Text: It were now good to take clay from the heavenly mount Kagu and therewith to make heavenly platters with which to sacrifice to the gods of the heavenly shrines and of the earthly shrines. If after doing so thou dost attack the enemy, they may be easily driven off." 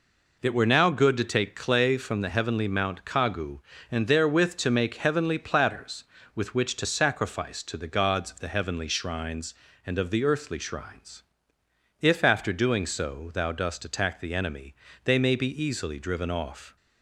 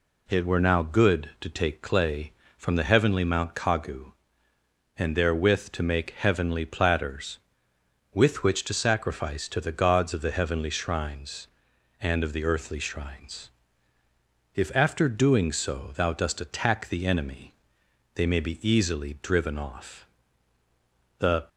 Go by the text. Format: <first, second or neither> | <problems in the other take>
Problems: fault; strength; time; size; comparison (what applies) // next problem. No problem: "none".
first | goes on to say "The"; slight; from 21.1 s on; 0.30 s long